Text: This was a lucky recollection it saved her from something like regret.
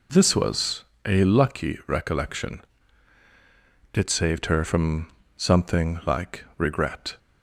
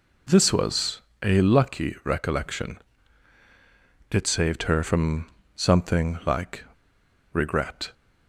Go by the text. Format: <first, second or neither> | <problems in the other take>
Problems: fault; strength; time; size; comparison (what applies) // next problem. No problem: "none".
first | pauses between "was" and "a"; slight; at 0.9 s; 0.24 s long; slight in the first // pauses between "recollection" and "it"; strong; at 2.7 s; 1.3 s long; strong in the first // pauses between "from" and "something"; slight; at 5.2 s; 0.26 s long; slight in the first // pauses between "like" and "regret"; noticeable; at 6.6 s; 0.67 s long